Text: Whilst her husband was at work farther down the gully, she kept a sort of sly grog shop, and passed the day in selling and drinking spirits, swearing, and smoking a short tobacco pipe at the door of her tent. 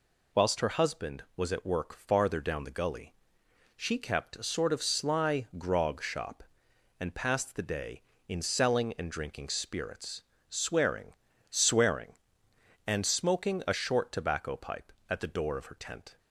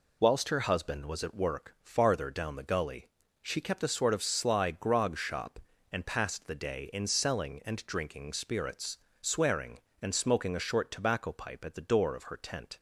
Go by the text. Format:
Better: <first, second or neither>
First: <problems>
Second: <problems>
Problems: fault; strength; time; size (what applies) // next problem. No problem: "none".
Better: second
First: says "swearing" twice; at 11.5 s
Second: none